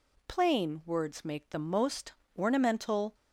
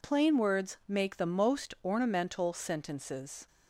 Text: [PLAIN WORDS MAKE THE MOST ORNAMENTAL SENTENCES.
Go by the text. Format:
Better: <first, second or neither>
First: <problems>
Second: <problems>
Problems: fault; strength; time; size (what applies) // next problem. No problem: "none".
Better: second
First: pauses between "MOST" and "ORNAMENTAL"; slight; at 2.1 s; 0.22 s long // stops before "SENTENCES"; at 3.1 s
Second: none